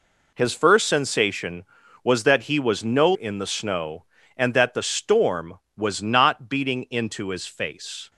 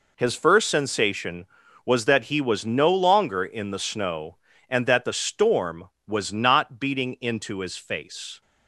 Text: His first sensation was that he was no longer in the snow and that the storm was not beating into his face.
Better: second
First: skips "longer"; at 3.1 s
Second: none

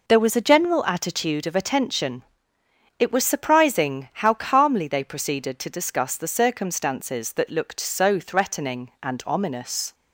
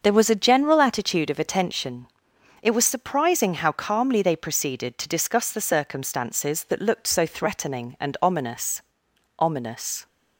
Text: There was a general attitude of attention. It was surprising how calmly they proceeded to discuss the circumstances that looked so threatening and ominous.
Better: first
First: none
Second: starts louder than the rest; until 1.0 s; 6.5 dB // says "ominous" twice; at 9.3 s

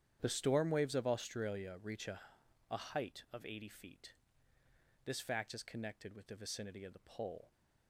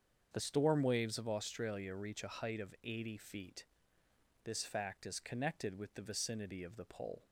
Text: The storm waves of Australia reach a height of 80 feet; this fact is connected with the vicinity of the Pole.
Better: second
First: starts louder than the rest; strong; until 1.2 s; 9.5 dB // says "a" twice; at 2.6 s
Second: starts louder than the rest; until 1.3 s; 7 dB

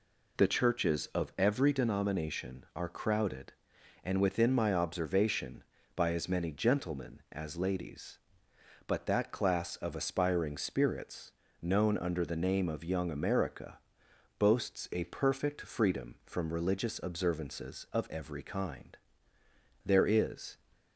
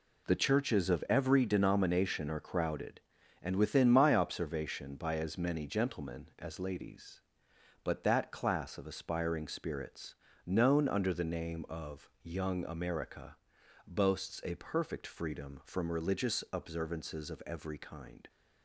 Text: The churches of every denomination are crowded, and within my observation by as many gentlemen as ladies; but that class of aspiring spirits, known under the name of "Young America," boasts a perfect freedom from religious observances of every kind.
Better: second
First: goes on to say "There is"; noticeable; from 19.8 s on; 0.72 s long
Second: none

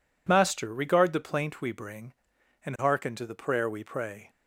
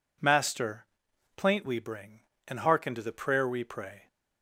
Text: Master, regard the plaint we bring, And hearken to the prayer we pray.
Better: first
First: none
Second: skips "regard the"; at 1.1 s

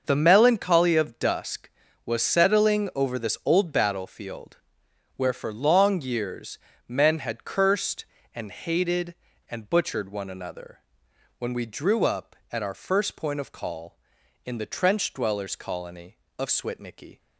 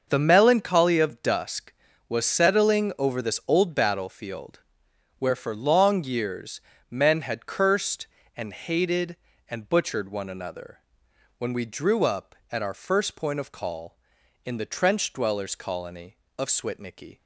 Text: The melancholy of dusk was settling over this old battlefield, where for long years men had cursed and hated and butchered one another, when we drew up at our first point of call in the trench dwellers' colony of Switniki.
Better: neither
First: starts louder than the rest; until 1.0 s; 6 dB // pauses between "years" and "men"; slight; at 6.5 s; 0.28 s long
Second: starts louder than the rest; until 1.0 s; 6 dB // pauses between "years" and "men"; slight; at 6.6 s; 0.28 s long

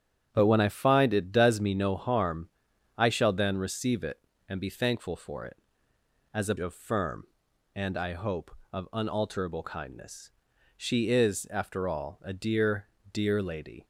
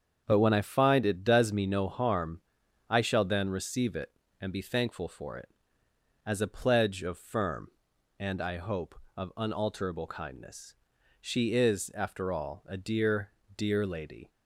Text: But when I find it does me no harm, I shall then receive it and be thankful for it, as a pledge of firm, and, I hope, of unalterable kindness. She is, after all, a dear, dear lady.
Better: second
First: starts louder than the rest; strong; until 1.3 s; 8.5 dB // skips "pledge"; at 6.5 s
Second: starts louder than the rest; strong; until 1.2 s; 7 dB

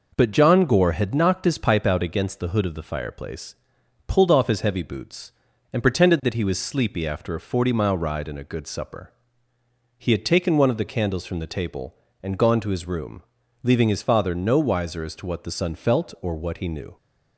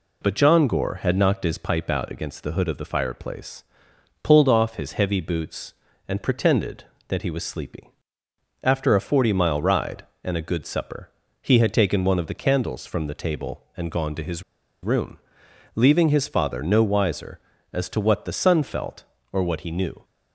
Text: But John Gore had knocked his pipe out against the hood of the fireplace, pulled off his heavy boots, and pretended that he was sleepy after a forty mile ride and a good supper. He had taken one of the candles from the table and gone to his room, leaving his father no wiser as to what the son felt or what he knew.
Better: first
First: none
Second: pauses between "sleepy" and "after"; noticeable; at 7.8 s; 0.74 s long // pauses between "his" and "room"; at 14.4 s; 0.40 s long

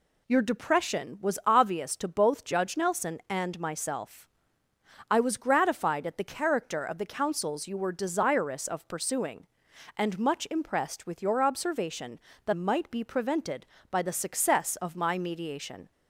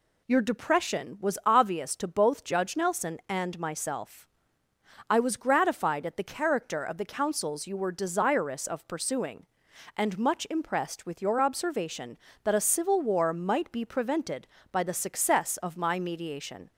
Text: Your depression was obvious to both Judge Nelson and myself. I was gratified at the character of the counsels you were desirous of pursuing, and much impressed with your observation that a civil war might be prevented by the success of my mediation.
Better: second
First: skips "a civil war"; at 12.5 s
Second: none

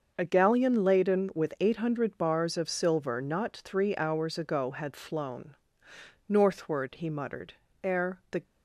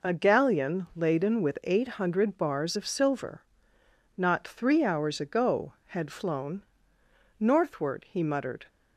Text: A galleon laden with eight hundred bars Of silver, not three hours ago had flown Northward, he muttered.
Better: second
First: starts louder than the rest; until 1.1 s; 6 dB // pauses between "flown" and "Northward"; noticeable; at 5.5 s; 0.74 s long // goes on to say "Ere the"; from 7.8 s on; 0.58 s long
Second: pauses between "flown" and "Northward"; noticeable; at 6.6 s; 0.78 s long

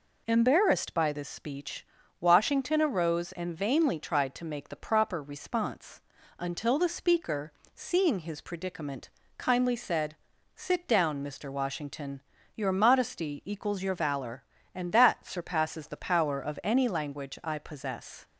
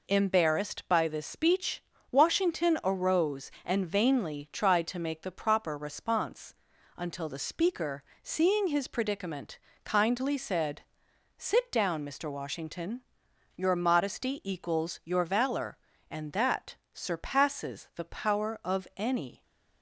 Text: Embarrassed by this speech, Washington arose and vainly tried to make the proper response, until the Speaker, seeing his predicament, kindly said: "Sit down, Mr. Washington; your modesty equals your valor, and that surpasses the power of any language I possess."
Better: first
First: none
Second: pauses between "that" and "surpasses"; slight; at 16.7 s; 0.16 s long // stops before "language I possess"; at 19.4 s

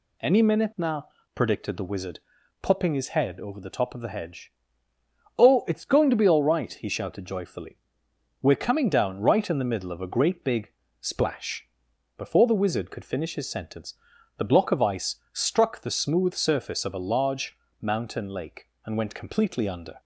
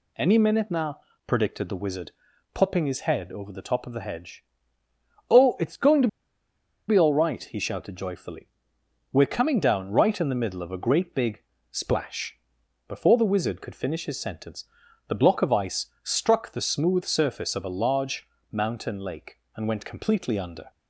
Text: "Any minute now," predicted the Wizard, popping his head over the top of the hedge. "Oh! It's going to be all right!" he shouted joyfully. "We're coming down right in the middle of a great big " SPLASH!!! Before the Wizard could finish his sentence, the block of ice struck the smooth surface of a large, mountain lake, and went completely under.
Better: first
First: pauses between "ice" and "struck"; slight; at 15.1 s; 0.16 s long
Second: pauses between "to" and "be"; noticeable; at 6.0 s; 0.80 s long // pauses between "ice" and "struck"; slight; at 15.8 s; 0.16 s long

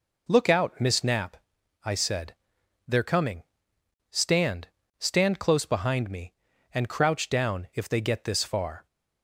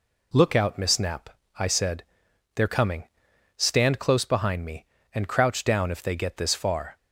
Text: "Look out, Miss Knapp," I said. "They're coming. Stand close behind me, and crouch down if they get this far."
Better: second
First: says "Stand" twice; at 5.0 s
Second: none

